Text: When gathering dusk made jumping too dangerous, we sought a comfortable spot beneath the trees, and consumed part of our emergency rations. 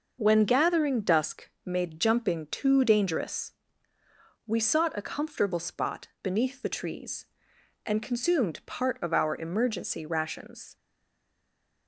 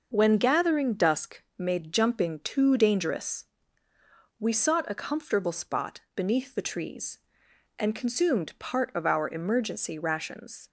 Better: second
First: starts louder than the rest; noticeable; until 1.2 s; 6 dB // pauses between "dusk" and "made"; slight; at 1.4 s; 0.16 s long // stays silent after the last word; from 10.7 s on; 1.1 s long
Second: starts louder than the rest; noticeable; until 1.1 s; 6 dB // pauses between "dusk" and "made"; slight; at 1.4 s; 0.16 s long

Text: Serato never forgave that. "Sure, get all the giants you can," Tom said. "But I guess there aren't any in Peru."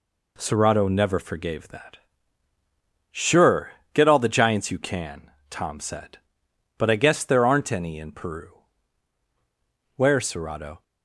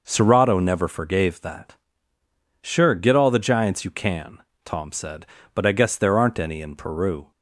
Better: second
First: goes on to say "Where Serato"; noticeable; from 9.9 s on; 0.88 s long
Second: none

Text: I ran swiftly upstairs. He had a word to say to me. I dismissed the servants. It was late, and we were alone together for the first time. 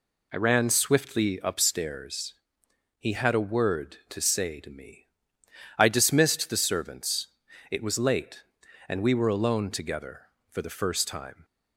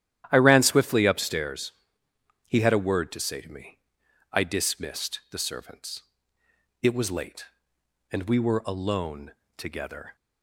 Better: first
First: none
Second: starts louder than the rest; strong; until 1.3 s; 11.5 dB // pauses between "alone" and "together"; slight; at 9.3 s; 0.26 s long // stops before "for the first time"; at 10.1 s

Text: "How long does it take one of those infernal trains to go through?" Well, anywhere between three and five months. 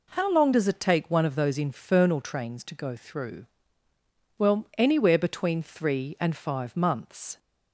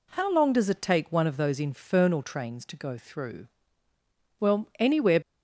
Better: first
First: none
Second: stops before "between three and five months"; at 5.2 s

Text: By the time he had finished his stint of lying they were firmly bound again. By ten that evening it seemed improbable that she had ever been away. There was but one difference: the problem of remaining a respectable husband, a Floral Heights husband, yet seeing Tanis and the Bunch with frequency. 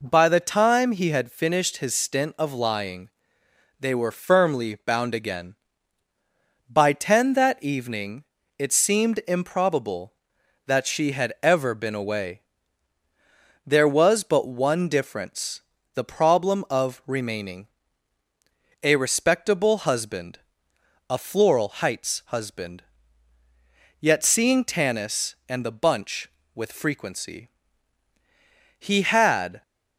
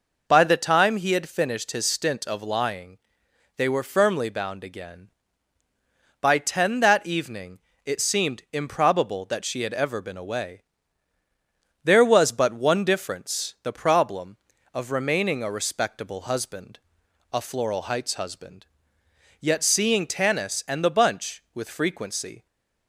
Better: second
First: pauses between "lying" and "they"; noticeable; at 3.0 s; 0.70 s long // pauses between "evening" and "it"; slight; at 8.2 s; 0.34 s long // pauses between "remaining" and "a"; at 17.6 s; 1.1 s long // goes on to say "He had"; noticeable; from 28.7 s on; 0.82 s long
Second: pauses between "lying" and "they"; noticeable; at 2.9 s; 0.58 s long // pauses between "evening" and "it"; slight; at 7.5 s; 0.28 s long

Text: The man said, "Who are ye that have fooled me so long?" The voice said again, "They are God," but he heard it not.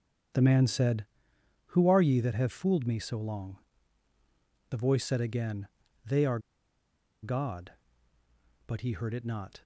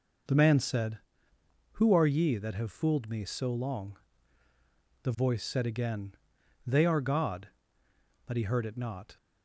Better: second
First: starts louder than the rest; strong; until 1.9 s; 7.5 dB // pauses between "are" and "God"; noticeable; at 6.3 s; 0.84 s long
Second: none

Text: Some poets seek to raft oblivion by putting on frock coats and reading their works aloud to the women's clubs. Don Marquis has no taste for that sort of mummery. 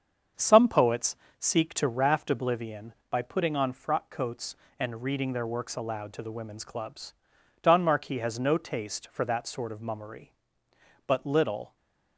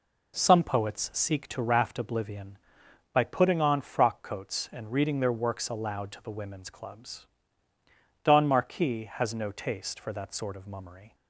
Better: second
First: starts louder than the rest; strong; until 1.6 s; 7 dB // pauses between "poets" and "seek"; slight; at 1.1 s; 0.24 s long // goes on to say "But little"; noticeable; from 11.0 s on; 0.70 s long // stays silent after the last word; slight; from 11.6 s on; 0.5 s long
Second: none

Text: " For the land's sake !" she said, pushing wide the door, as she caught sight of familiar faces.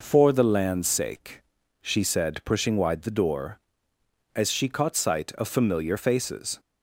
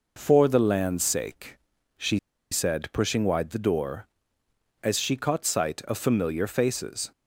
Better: first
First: none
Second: pauses between "she" and "said"; slight; at 2.1 s; 0.34 s long

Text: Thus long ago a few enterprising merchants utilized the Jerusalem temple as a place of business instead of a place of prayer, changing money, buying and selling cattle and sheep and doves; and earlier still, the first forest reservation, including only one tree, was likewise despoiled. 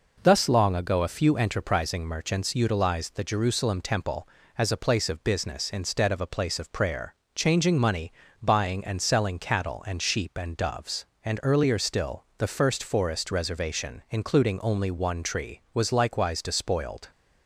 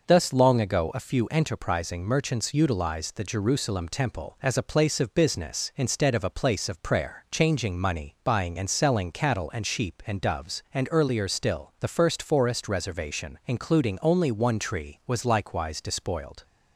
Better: neither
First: none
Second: none

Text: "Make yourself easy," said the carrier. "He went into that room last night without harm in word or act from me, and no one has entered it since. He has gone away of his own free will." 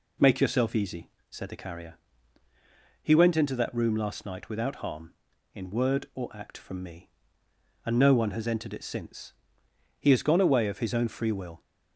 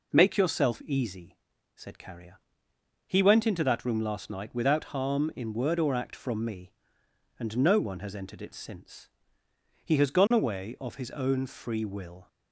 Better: first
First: none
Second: skips "the"; at 1.9 s

